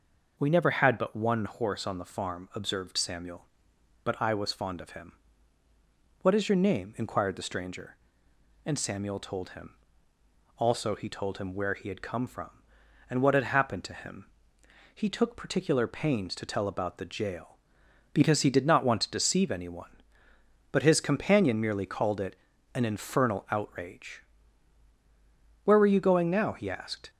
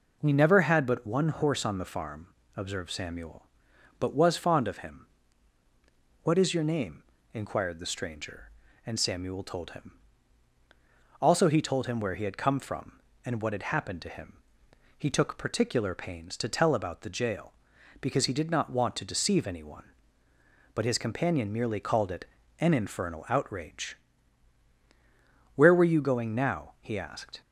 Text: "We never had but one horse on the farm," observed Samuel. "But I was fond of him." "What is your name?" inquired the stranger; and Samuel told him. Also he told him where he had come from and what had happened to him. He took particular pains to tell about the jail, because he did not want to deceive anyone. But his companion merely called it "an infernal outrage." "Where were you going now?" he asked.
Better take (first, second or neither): first